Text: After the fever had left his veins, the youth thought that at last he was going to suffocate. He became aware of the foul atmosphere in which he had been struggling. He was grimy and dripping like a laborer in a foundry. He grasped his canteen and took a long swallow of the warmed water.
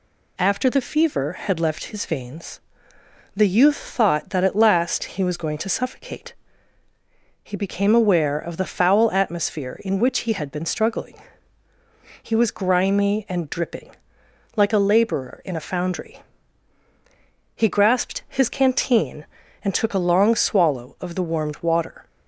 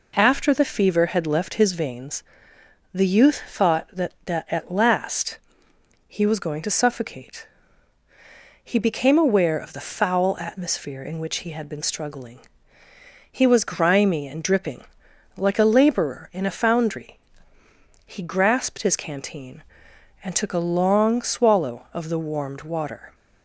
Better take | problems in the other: first | says "that" twice; at 4.2 s // pauses between "last" and "he"; noticeable; at 5.3 s; 0.68 s long // pauses between "dripping" and "like"; noticeable; at 14.8 s; 0.52 s long; noticeable in the first

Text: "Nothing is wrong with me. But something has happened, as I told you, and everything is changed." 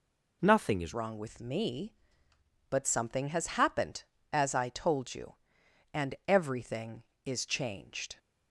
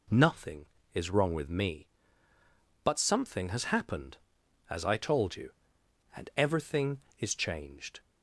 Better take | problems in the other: second | changes voice at "wrong"; from 0.9 s on; 7.2 s long

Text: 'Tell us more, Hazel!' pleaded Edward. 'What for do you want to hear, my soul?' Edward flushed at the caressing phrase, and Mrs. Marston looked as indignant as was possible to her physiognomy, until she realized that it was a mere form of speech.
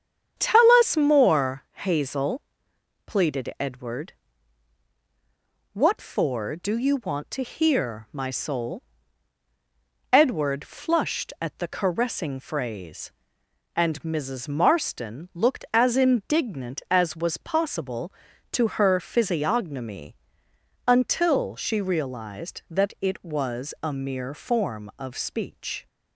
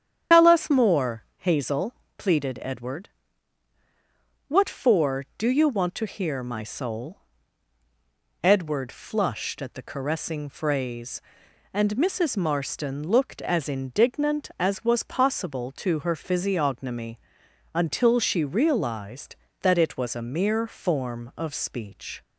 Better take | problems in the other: first | loses the start of "Tell"; at 0.3 s; 125 ms // starts louder than the rest; strong; until 1.4 s; 9 dB; strong in the first

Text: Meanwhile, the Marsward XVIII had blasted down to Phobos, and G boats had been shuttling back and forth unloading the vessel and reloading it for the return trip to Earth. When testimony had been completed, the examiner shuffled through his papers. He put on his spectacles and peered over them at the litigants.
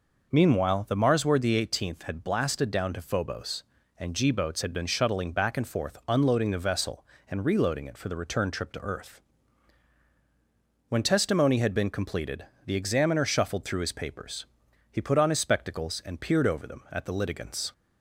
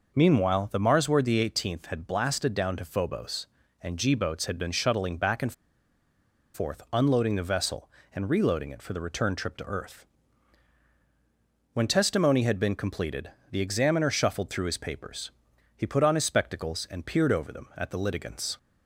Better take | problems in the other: first | pauses between "and" and "forth"; at 5.5 s; 1.0 s long

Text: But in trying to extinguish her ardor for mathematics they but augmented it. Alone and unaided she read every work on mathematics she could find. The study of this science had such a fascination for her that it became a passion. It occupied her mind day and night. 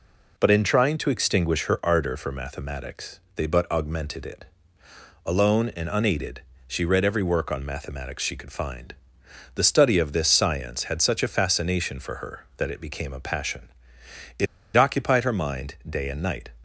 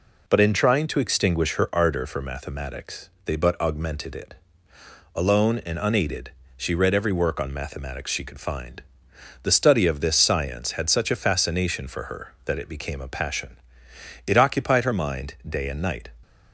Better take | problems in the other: second | pauses between "mathematics" and "they"; slight; at 3.2 s; 0.16 s long; slight in the second // pauses between "unaided" and "she"; slight; at 6.4 s; 0.26 s long; slight in the second // pauses between "It" and "occupied"; slight; at 14.4 s; 0.29 s long

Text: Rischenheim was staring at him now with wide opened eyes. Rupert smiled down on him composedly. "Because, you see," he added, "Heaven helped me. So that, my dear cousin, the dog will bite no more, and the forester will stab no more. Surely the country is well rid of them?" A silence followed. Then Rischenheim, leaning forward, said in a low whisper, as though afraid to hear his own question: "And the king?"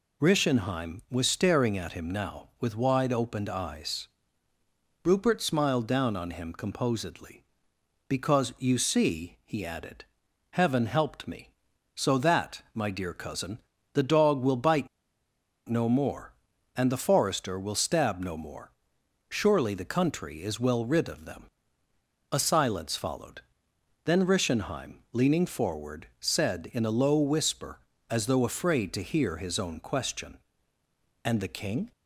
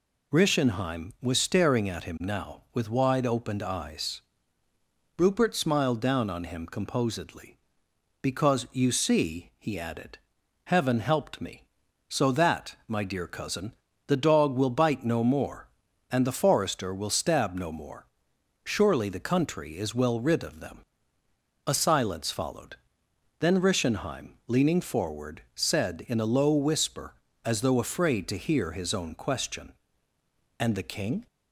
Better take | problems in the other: second | pauses between "bite" and "no"; noticeable; at 14.8 s; 0.81 s long

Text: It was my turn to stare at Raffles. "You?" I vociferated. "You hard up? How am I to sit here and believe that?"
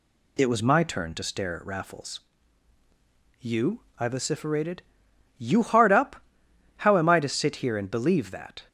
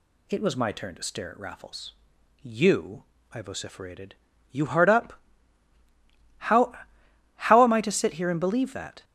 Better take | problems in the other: first | says "How" twice; at 7.3 s

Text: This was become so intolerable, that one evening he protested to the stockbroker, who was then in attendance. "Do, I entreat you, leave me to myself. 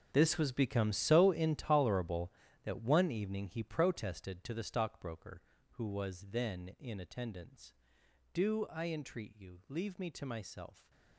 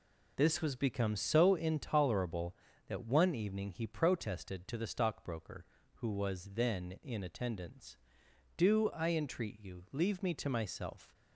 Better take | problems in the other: second | gets quieter; strong; throughout; 14.5 dB

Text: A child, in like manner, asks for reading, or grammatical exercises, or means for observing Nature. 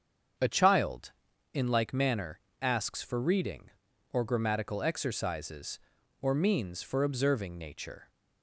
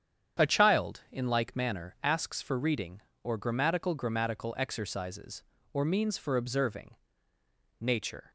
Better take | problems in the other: first | starts louder than the rest; strong; until 1.4 s; 8.5 dB; strong in the first // says "grammatical" twice; at 3.9 s // pauses between "observing" and "Nature"; noticeable; at 6.9 s; 0.86 s long

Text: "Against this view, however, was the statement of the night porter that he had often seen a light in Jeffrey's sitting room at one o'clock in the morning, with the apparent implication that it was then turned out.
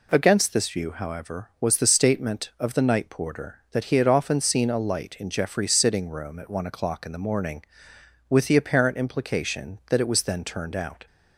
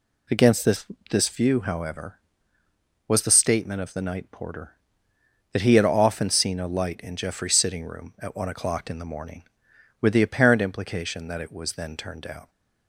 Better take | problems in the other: first | says "this" twice; at 1.0 s

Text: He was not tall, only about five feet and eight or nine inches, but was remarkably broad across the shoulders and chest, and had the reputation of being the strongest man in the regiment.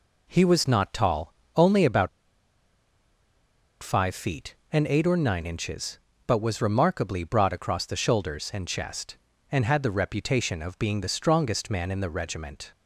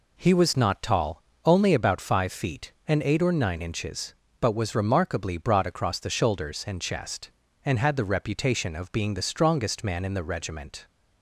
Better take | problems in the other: second | pauses between "about" and "five"; strong; at 2.0 s; 1.7 s long

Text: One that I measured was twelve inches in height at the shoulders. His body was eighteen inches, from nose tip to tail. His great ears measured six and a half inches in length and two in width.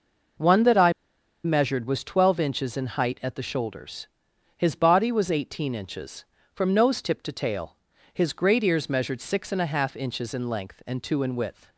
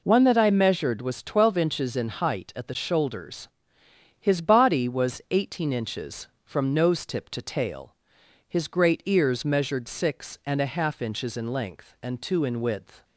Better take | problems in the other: second | pauses between "I" and "measured"; noticeable; at 0.9 s; 0.52 s long

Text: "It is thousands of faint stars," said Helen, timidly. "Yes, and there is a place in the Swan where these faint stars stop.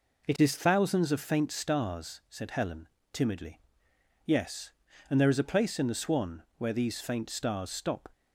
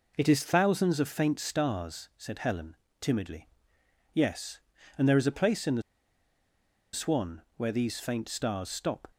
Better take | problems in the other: first | pauses between "the" and "Swan"; at 5.8 s; 1.1 s long // pauses between "Swan" and "where"; slight; at 7.4 s; 0.16 s long; slight in the first

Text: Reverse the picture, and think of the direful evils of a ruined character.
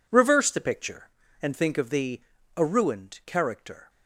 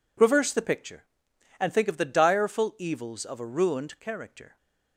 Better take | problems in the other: second | skips "direful evils of"; at 2.3 s

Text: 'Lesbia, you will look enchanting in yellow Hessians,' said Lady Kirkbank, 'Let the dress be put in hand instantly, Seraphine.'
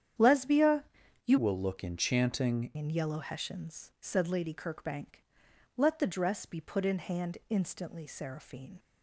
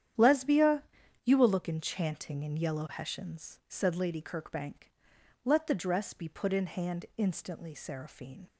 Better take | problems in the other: second | starts louder than the rest; strong; until 1.6 s; 9.5 dB; strong in the second // changes voice from "will" to "enchanting"; from 1.3 to 2.7 s; 1.4 s long

